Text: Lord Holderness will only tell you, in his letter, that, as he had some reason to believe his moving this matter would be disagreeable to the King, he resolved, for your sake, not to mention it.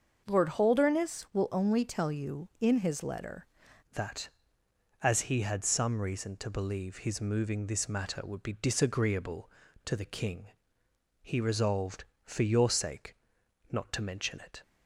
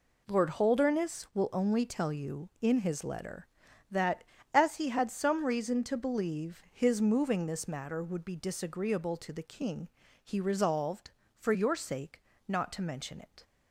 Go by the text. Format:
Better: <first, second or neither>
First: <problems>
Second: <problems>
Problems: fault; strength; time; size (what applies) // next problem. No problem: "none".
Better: second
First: starts louder than the rest; until 1.2 s; 6.5 dB // changes voice at "that"; from 3.9 s on; 10.7 s long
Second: none